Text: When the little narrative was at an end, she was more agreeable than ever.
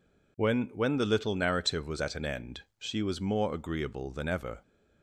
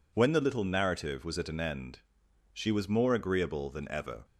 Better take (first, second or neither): second